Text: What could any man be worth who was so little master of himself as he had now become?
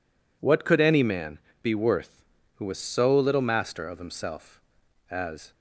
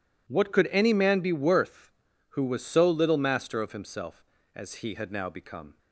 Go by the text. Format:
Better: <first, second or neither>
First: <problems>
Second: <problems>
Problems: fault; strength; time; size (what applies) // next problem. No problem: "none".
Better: second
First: pauses between "man" and "be"; slight; at 1.3 s; 0.24 s long // stops before "he had now become"; at 5.5 s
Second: none